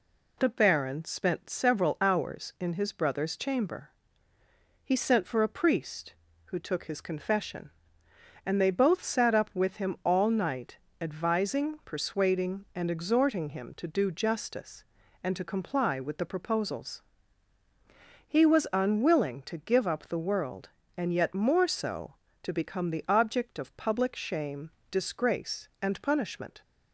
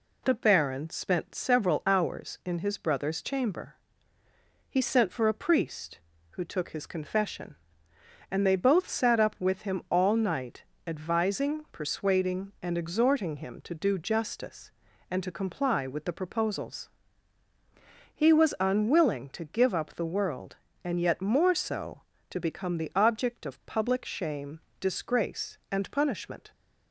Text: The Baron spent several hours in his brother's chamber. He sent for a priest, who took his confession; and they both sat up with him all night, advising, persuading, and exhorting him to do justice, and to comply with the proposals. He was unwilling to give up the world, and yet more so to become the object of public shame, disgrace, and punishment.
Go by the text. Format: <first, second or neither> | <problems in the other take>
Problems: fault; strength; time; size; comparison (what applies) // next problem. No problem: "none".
neither | none